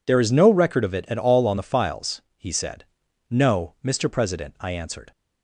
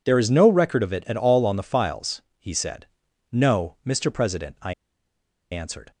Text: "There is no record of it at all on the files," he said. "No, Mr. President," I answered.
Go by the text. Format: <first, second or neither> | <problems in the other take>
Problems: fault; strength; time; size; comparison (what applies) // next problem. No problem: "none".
first | pauses between "I" and "answered"; noticeable; at 4.7 s; 0.78 s long